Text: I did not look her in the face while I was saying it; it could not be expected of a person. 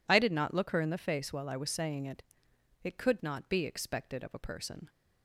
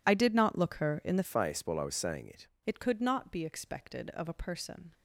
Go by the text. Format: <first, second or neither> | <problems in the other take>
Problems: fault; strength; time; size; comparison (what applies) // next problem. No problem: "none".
first | changes voice from "face" to "it"; from 1.2 to 2.4 s; 1.2 s long